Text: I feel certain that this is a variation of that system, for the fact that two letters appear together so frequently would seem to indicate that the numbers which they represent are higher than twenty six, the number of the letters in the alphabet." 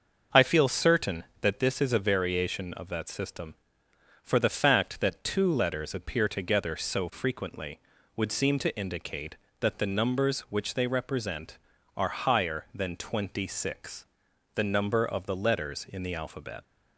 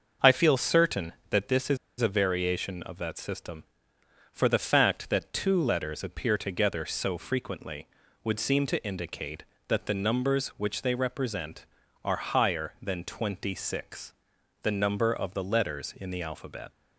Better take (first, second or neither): first